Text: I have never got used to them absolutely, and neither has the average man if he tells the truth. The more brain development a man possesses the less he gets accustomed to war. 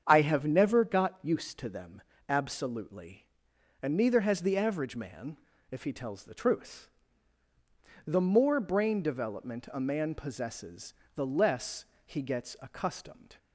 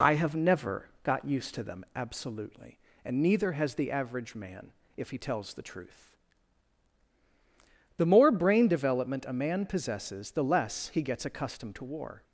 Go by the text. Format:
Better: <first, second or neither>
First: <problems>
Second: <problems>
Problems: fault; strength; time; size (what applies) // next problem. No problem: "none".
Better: second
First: starts louder than the rest; strong; until 1.0 s; 8 dB // pauses between "them" and "absolutely"; slight; at 2.0 s; 0.26 s long // pauses between "man" and "if"; slight; at 5.3 s; 0.32 s long // pauses between "possesses" and "the"; slight; at 10.9 s; 0.22 s long // pauses between "less" and "he"; slight; at 11.8 s; 0.20 s long // stops before "to war"; at 13.3 s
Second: pauses between "man" and "if"; slight; at 4.7 s; 0.26 s long